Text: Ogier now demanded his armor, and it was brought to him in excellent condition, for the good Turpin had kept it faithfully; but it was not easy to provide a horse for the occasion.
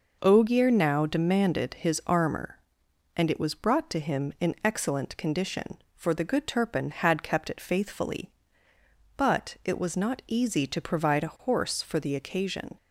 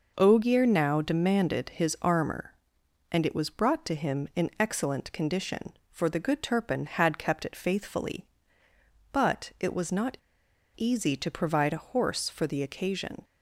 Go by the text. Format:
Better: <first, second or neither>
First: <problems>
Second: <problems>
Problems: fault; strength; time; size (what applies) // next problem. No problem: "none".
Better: first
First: none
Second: pauses between "not" and "easy"; noticeable; at 10.1 s; 0.58 s long